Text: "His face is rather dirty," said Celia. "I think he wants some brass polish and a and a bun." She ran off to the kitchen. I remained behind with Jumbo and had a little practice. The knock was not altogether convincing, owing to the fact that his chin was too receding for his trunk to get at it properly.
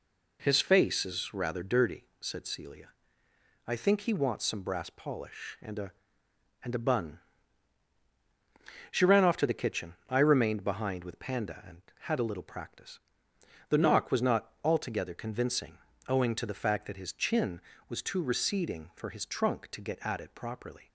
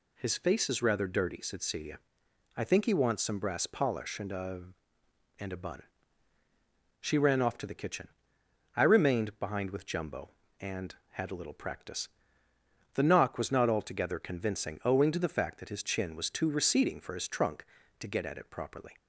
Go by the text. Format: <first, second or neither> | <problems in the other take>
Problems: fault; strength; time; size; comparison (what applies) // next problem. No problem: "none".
second | says "Panda" for "Jumbo"; at 11.1 s